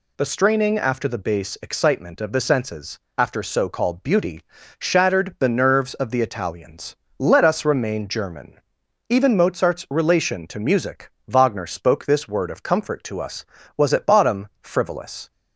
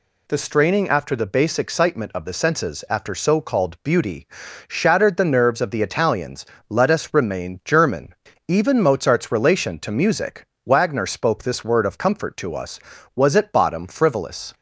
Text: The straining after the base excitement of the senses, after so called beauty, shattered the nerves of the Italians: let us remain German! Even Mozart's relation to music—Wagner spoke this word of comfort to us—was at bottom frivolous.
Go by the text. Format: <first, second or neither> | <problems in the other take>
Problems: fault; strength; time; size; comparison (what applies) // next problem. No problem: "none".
neither | none